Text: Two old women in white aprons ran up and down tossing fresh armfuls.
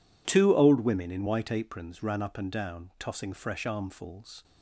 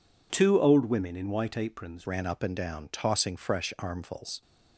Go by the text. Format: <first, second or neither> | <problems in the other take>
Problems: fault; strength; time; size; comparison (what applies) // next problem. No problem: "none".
first | changes voice at "ran"; from 2.0 s on; 2.4 s long